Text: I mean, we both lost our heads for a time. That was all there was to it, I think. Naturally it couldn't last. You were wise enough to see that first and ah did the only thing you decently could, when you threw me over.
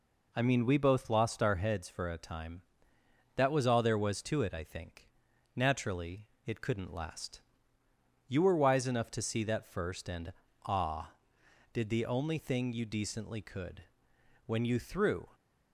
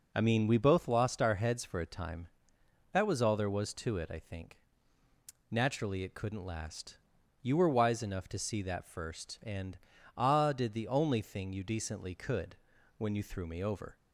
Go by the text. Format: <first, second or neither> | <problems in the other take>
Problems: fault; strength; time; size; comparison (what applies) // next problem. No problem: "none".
second | pauses between "Naturally" and "it"; slight; at 6.2 s; 0.20 s long // pauses between "and" and "ah"; slight; at 10.3 s; 0.32 s long; also in the second // stops before "me over"; at 15.3 s